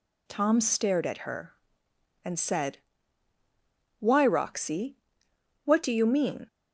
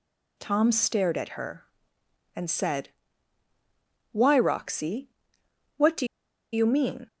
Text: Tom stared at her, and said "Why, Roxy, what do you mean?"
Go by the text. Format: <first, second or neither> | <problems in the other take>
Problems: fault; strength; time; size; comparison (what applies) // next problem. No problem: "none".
first | pauses between "said" and "Why"; at 2.8 s; 1.2 s long; also in the first // pauses between "do" and "you"; noticeable; at 6.0 s; 0.47 s long